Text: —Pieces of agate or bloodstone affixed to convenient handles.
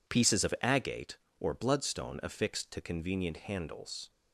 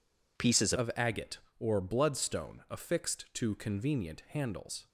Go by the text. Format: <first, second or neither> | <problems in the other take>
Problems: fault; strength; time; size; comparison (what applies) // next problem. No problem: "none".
first | changes voice at "of"; from 0.7 s on; 4.1 s long